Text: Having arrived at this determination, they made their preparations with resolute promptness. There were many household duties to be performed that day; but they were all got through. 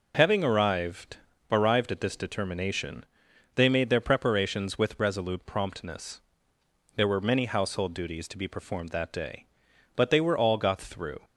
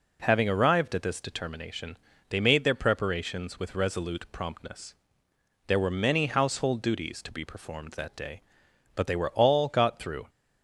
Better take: second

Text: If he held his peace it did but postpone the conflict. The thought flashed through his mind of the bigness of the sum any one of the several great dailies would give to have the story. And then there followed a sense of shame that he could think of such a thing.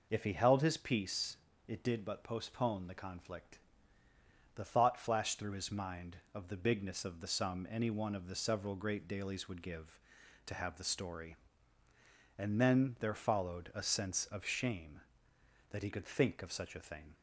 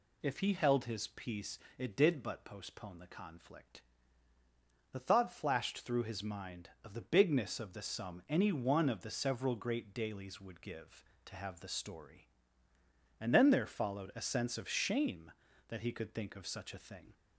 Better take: neither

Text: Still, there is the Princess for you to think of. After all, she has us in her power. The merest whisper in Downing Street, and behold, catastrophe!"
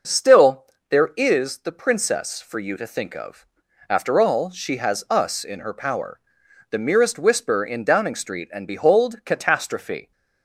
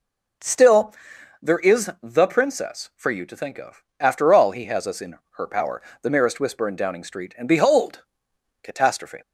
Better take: first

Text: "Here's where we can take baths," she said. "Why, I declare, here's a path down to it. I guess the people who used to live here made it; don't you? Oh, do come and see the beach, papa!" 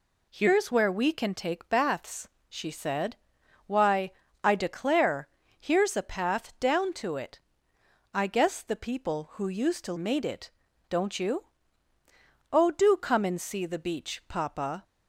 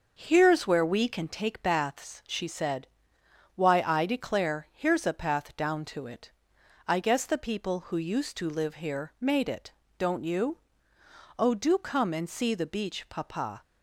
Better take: second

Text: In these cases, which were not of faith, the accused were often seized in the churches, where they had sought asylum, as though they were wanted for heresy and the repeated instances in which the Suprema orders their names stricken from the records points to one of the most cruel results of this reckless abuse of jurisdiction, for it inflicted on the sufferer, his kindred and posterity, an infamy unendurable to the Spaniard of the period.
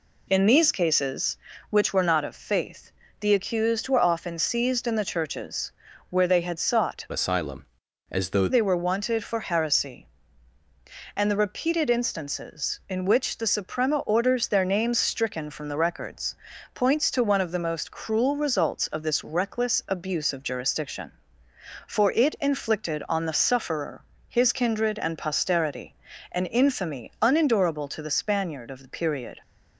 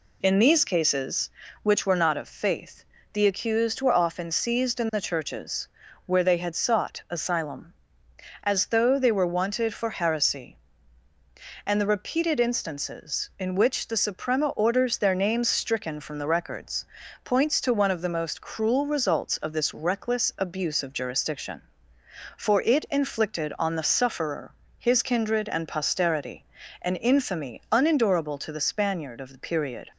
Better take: second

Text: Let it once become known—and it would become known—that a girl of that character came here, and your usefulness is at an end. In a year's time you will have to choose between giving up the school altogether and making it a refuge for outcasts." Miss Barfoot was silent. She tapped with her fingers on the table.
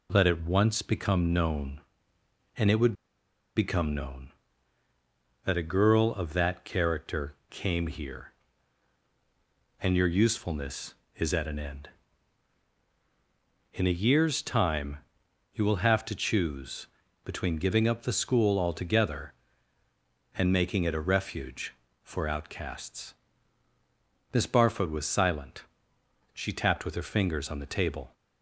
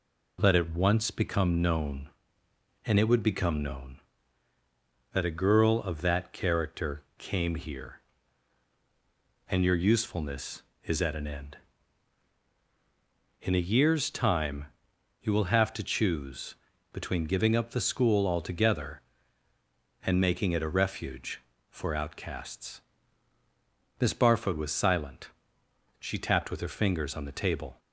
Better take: second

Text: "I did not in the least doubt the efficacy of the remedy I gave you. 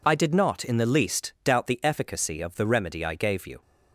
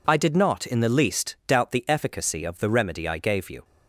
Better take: neither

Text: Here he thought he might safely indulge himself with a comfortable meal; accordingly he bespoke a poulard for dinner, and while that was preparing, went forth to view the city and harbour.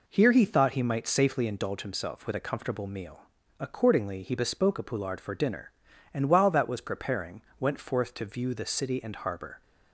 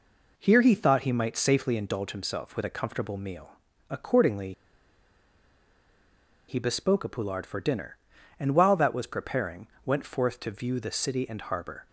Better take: first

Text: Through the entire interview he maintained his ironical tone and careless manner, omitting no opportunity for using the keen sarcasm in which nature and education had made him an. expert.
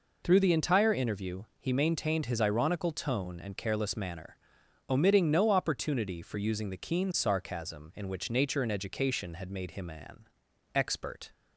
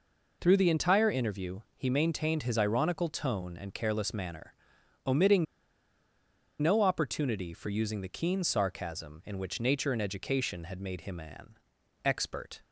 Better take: first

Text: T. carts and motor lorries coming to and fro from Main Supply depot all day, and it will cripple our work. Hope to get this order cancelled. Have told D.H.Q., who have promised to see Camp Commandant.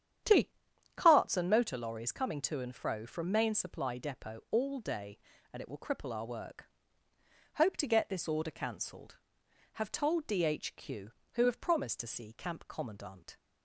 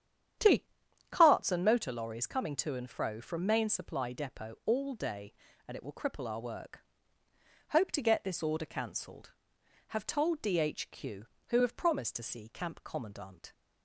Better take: neither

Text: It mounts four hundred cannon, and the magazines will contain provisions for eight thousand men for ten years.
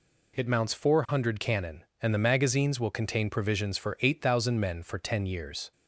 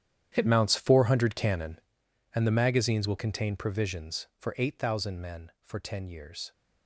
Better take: first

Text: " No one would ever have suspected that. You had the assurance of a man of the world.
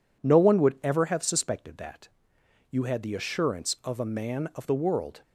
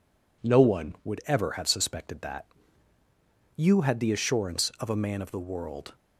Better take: neither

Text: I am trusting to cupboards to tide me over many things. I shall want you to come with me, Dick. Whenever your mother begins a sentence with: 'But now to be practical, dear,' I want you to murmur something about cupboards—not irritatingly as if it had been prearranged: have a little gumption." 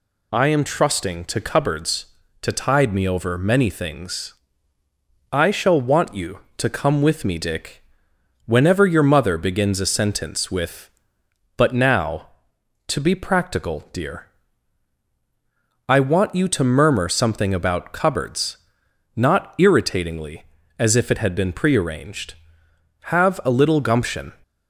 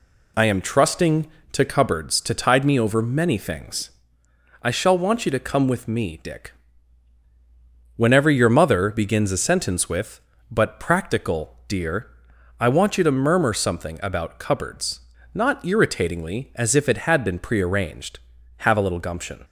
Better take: first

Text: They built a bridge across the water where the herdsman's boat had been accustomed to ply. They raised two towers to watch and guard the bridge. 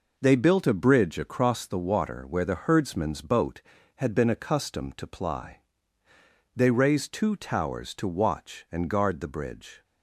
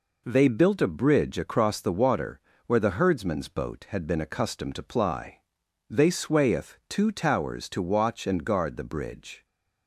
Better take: first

